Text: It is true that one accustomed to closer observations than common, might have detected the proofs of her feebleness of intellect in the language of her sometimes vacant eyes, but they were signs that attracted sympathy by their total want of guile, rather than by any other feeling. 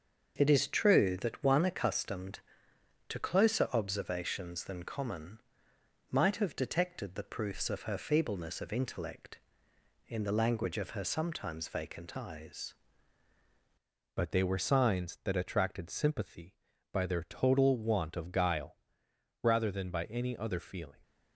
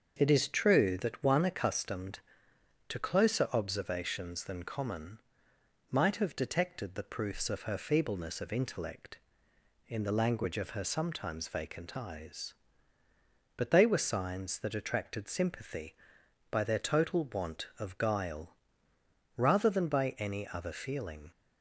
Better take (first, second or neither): second